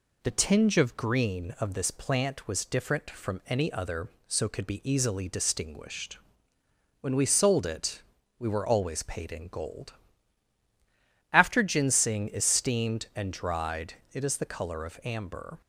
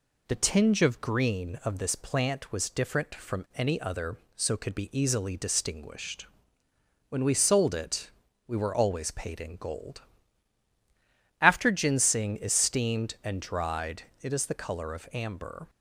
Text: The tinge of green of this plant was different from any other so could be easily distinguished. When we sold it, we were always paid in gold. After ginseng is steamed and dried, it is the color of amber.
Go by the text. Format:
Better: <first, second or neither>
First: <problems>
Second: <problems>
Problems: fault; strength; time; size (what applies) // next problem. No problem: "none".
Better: neither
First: none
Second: none